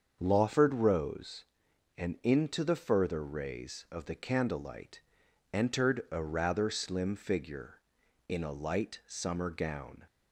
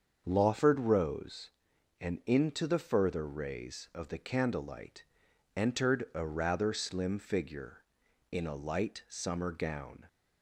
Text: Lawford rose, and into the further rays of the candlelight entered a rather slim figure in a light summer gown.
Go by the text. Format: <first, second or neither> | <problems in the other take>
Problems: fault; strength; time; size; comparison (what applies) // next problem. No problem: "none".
neither | starts louder than the rest; the same in both // pauses between "candlelight" and "entered"; noticeable; the same in both